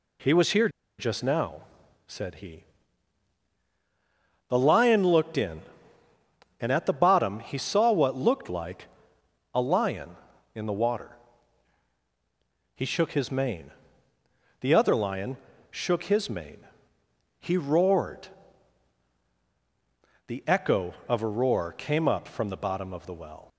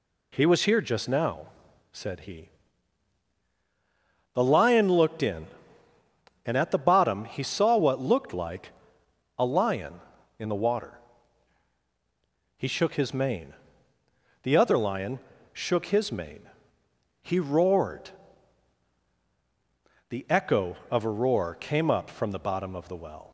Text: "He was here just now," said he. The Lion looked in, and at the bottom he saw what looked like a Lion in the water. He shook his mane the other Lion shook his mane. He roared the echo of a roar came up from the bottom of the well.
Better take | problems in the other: second | pauses between "here" and "just"; slight; at 0.6 s; 0.29 s long // pauses between "like" and "a"; noticeable; at 8.8 s; 0.66 s long; noticeable in the second // pauses between "mane" and "the"; noticeable; at 13.7 s; 0.88 s long; noticeable in the second // pauses between "Lion" and "shook"; slight; at 15.3 s; 0.34 s long; slight in the second // pauses between "roared" and "the"; strong; at 18.2 s; 2.0 s long; strong in the second

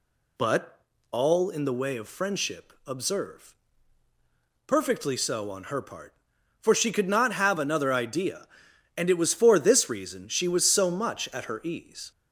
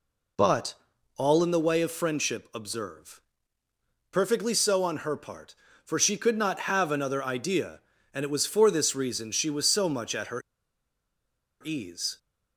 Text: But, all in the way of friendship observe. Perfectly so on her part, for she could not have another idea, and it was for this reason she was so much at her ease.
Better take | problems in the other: first | pauses between "her" and "ease"; at 10.4 s; 1.2 s long

